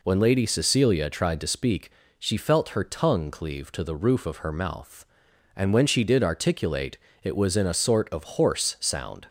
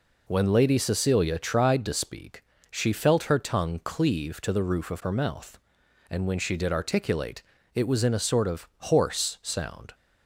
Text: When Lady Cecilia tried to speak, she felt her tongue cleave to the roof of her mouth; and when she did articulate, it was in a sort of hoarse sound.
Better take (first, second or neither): neither